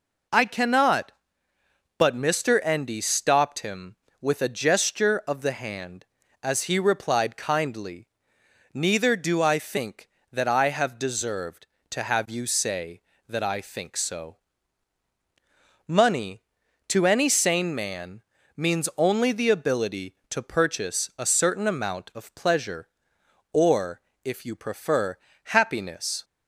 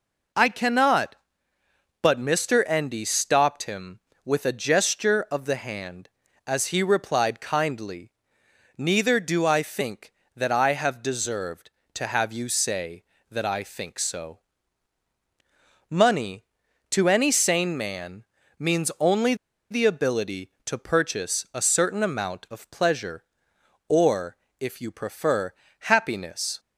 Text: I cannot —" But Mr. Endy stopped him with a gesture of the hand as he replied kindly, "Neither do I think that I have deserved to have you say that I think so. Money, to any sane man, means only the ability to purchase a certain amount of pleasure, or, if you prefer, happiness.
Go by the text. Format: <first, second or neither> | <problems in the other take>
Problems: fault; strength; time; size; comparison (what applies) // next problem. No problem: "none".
first | pauses between "only" and "the"; at 19.3 s; 0.36 s long